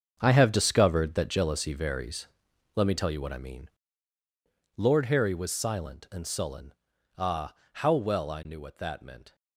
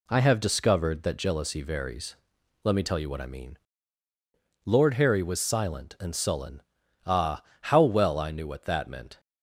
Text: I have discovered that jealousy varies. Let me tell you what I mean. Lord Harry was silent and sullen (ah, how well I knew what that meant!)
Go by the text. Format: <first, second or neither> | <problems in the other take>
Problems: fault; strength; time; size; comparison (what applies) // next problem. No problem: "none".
second | gets quieter; strong; throughout; 12 dB